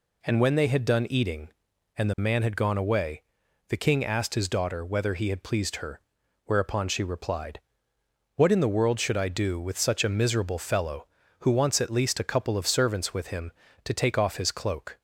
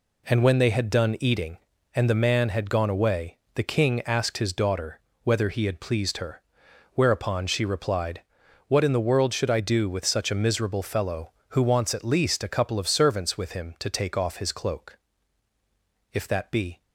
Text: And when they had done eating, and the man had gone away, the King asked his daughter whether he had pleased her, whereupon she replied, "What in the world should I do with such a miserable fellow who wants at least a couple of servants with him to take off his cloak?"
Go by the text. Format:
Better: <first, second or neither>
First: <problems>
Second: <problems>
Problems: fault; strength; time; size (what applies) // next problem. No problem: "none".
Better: first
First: none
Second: pauses between "daughter" and "whether"; slight; at 4.9 s; 0.24 s long // goes on to say "If that be"; noticeable; from 16.1 s on; 0.70 s long